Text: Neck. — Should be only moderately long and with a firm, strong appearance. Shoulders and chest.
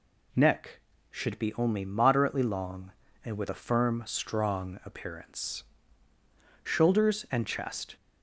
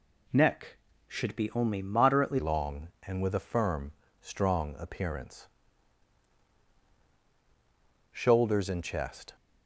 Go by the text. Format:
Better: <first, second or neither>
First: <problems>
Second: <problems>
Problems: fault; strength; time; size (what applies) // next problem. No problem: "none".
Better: first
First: none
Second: changes voice at "long"; from 2.3 s on; 7.0 s long